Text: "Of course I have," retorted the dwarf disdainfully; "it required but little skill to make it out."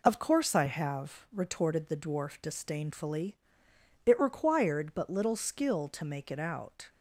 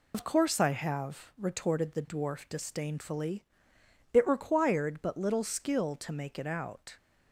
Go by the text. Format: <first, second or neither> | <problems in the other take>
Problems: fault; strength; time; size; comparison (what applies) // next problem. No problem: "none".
first | loses the start of "Of"; at 0.1 s; 60 ms